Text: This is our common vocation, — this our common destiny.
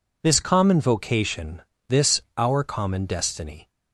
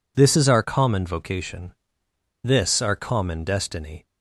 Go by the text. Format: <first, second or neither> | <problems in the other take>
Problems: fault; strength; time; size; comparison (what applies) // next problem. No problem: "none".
second | skips "is our"; at 0.3 s // pauses between "this" and "our"; slight; at 2.1 s; 0.16 s long